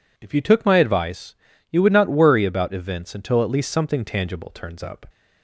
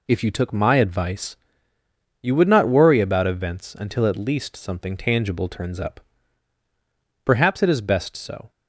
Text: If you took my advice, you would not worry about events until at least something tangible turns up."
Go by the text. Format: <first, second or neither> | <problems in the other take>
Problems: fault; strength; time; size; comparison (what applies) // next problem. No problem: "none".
first | goes on to say "Perhaps it is best so"; noticeable; from 7.2 s on; 1.2 s long